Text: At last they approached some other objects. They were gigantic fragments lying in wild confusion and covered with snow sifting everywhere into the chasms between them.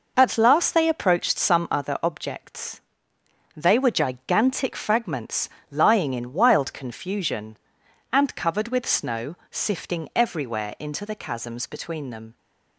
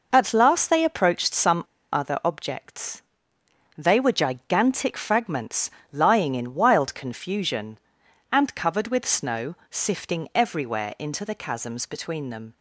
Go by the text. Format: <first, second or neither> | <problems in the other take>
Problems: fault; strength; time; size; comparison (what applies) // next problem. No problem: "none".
first | pauses between "some" and "other"; slight; at 1.6 s; 0.29 s long // pauses between "fragments" and "lying"; slight; at 5.7 s; 0.22 s long; slight in the first // pauses between "snow" and "sifting"; slight; at 9.5 s; 0.16 s long; slight in the first